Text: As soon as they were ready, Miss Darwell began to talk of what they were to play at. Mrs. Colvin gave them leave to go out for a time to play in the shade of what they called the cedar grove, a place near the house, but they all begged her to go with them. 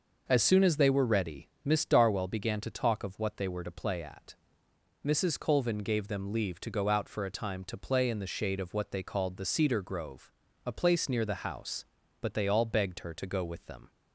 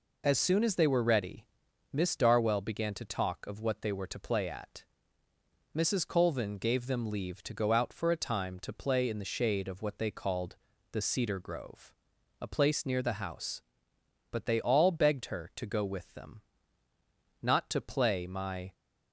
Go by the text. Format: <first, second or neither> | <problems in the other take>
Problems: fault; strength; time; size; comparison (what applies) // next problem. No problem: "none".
first | pauses between "called" and "the"; at 10.5 s; 0.38 s long // goes on to say "Not to play my"; noticeable; from 17.4 s on; 1.3 s long